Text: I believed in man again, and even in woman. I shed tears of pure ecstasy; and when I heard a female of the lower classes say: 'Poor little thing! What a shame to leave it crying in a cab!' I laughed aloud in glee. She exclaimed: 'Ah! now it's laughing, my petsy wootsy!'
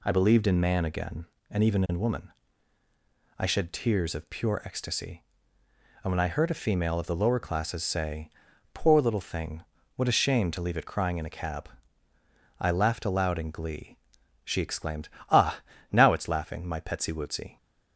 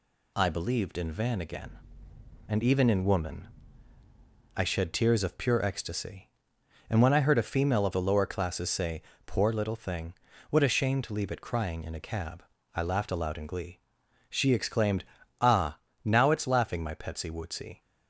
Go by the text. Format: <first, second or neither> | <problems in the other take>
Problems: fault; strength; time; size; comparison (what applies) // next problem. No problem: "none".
first | says "van" for "man"; at 1.1 s